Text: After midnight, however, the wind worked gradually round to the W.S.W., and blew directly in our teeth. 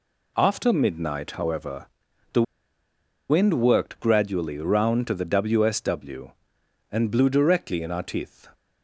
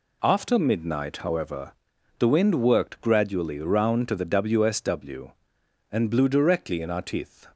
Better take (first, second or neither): second